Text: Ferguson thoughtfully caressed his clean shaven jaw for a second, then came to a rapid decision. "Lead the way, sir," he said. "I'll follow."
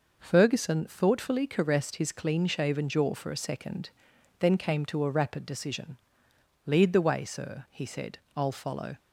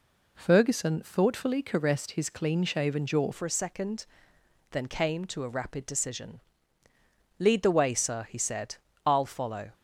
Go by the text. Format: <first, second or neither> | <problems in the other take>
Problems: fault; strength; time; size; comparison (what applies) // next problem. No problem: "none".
first | changes voice at "for"; from 3.3 s on; 6.4 s long